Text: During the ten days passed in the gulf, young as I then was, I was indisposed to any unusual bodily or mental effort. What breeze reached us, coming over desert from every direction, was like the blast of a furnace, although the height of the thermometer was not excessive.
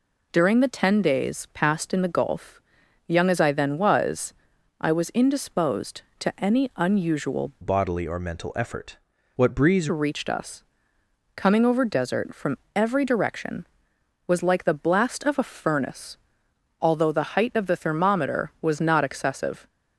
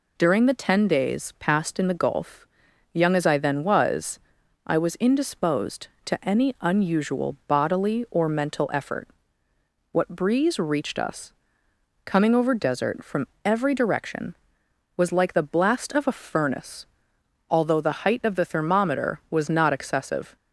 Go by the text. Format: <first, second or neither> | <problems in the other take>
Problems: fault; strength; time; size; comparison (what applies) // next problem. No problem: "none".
second | changes voice from "bodily" to "breeze"; from 7.6 to 9.8 s; 2.2 s long // pauses between "from" and "every"; slight; at 12.5 s; 0.18 s long; slight in the second